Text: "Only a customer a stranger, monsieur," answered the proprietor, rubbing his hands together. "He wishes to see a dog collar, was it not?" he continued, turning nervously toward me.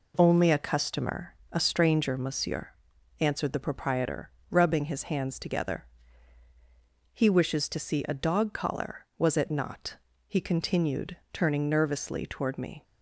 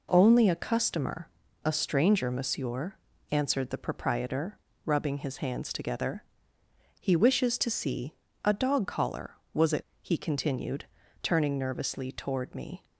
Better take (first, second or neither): first